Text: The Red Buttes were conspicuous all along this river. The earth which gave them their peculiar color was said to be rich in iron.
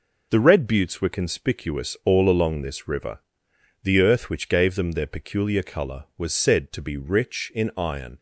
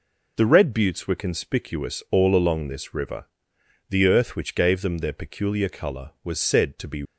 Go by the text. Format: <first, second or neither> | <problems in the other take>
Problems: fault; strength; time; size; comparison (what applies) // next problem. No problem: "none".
first | stops before "rich in iron"; at 7.0 s